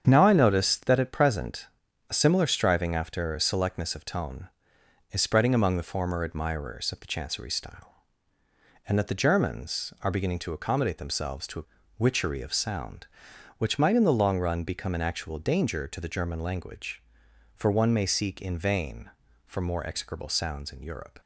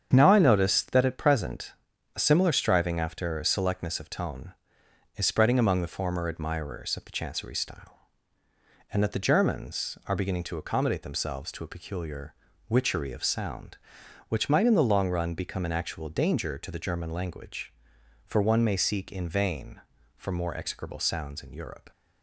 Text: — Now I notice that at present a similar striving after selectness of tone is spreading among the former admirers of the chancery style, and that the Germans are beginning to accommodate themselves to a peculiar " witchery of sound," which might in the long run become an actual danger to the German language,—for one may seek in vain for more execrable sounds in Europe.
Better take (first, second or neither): second